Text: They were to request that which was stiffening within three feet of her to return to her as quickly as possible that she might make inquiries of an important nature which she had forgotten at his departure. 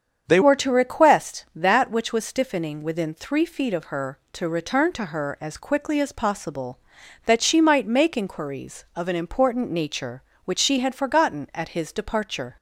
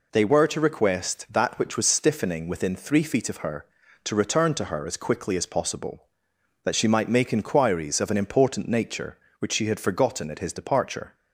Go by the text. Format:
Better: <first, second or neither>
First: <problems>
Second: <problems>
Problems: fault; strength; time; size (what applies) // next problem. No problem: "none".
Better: second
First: starts louder than the rest; strong; until 1.3 s; 7.5 dB // changes voice at "were"; from 0.4 s on; 12.1 s long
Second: none